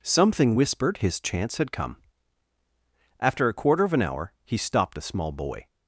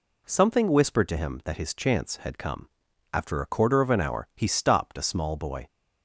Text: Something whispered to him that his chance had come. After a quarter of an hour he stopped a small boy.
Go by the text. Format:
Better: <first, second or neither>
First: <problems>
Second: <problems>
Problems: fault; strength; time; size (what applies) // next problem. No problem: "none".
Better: second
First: skips "to him that"; at 0.9 s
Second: none